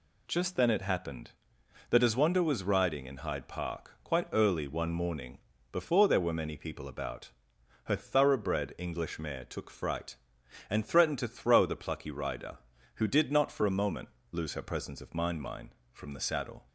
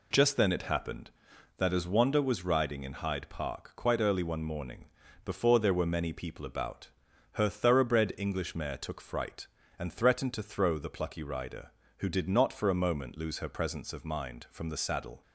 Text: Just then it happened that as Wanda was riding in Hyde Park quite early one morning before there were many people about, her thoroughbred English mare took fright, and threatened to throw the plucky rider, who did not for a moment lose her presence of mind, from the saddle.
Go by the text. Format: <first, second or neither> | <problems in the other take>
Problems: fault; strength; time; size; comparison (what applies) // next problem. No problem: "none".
second | pauses between "morning" and "before"; slight; at 5.3 s; 0.34 s long; also in the second // pauses between "moment" and "lose"; slight; at 14.0 s; 0.24 s long // says "mind" twice; at 15.4 s